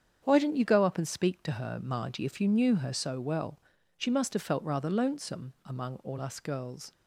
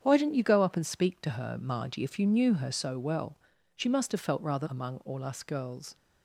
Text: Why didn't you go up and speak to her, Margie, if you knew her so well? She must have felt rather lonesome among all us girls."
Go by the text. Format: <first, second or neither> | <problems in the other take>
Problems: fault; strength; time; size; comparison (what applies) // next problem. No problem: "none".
first | starts louder than the rest; strong; until 1.0 s; 8 dB; strong in the first // skips "lonesome"; at 4.6 s